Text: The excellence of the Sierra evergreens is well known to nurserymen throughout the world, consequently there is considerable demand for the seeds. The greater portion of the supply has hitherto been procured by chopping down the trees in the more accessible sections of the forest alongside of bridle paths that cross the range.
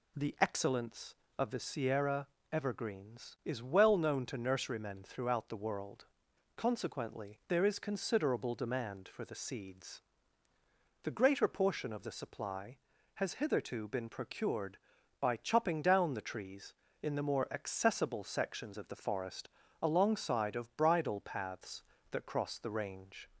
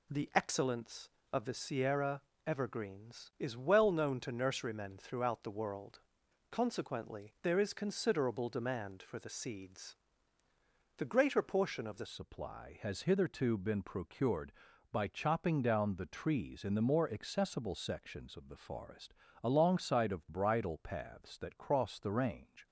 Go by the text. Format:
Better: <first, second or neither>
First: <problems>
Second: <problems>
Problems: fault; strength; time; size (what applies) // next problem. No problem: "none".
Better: first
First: pauses between "Sierra" and "evergreens"; slight; at 2.2 s; 0.24 s long // pauses between "forest" and "alongside"; slight; at 19.4 s; 0.32 s long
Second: pauses between "Sierra" and "evergreens"; slight; at 2.2 s; 0.24 s long // changes voice at "supply"; from 12.0 s on; 10.6 s long // pauses between "forest" and "alongside"; slight; at 19.1 s; 0.32 s long